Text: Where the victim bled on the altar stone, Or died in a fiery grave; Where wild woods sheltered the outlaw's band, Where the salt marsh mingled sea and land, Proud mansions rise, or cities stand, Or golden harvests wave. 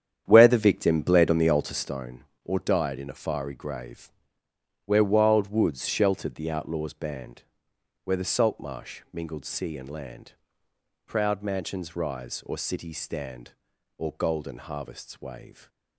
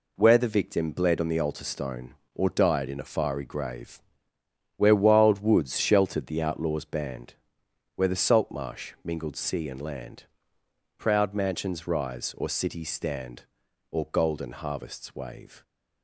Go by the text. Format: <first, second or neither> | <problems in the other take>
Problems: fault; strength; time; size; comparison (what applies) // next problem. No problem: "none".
second | starts louder than the rest; strong; until 2.0 s; 9 dB